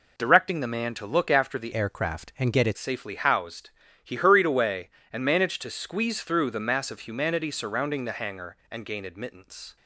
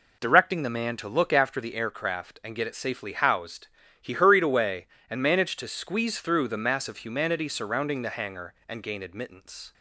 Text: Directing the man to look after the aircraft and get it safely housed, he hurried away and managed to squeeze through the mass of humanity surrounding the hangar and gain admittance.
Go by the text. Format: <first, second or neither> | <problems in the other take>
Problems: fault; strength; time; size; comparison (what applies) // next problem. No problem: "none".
second | changes voice from "aircraft" to "it"; from 1.7 to 2.7 s; 1.0 s long